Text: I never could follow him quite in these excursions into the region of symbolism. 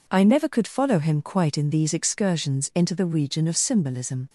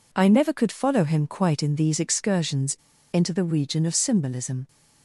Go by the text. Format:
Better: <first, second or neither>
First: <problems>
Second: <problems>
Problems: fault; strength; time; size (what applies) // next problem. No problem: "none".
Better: first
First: none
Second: pauses between "excursions" and "into"; at 2.7 s; 0.38 s long